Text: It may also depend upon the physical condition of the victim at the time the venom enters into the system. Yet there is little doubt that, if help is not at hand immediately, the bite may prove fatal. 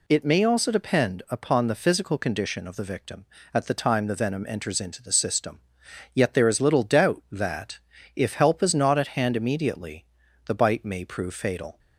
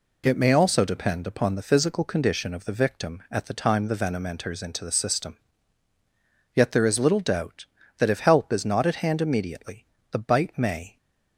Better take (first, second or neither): first